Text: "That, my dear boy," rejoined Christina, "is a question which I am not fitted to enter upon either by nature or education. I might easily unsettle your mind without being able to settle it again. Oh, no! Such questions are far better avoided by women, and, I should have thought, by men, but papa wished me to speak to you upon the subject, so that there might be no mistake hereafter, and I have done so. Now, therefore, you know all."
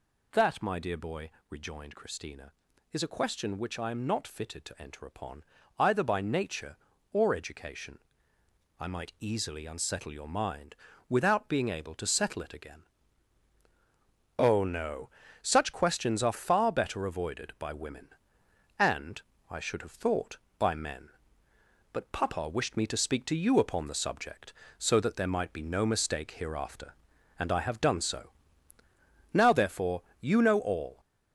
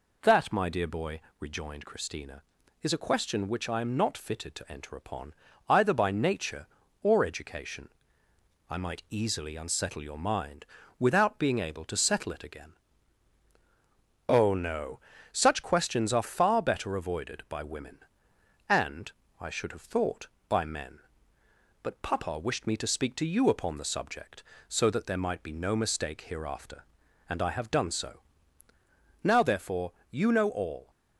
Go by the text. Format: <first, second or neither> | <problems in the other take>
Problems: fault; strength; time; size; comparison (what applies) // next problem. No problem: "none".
second | gets louder; noticeable; throughout; 5 dB // pauses between "upon" and "either"; slight; at 5.4 s; 0.36 s long; slight in the second // pauses between "mind" and "without"; slight; at 10.7 s; 0.32 s long; slight in the second